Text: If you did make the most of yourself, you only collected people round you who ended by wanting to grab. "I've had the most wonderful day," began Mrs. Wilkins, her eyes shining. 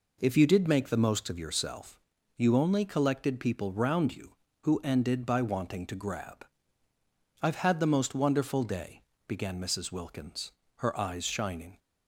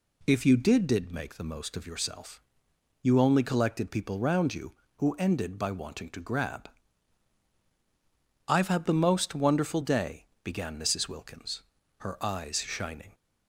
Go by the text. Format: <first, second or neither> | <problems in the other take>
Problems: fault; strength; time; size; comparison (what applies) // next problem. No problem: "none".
first | says "did" twice; at 0.8 s